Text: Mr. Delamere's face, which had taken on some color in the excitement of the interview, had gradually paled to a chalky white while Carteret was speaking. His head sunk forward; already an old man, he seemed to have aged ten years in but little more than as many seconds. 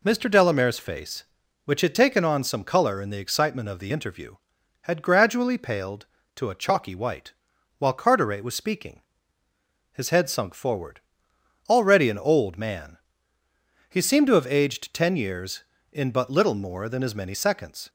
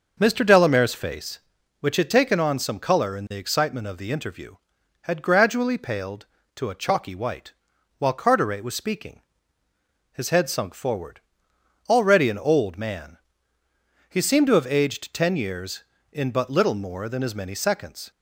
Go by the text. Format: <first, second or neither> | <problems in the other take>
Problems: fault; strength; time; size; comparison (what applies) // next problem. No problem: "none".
first | starts louder than the rest; noticeable; until 1.3 s; 6 dB // pauses between "white" and "while"; at 7.5 s; 0.44 s long; also in the first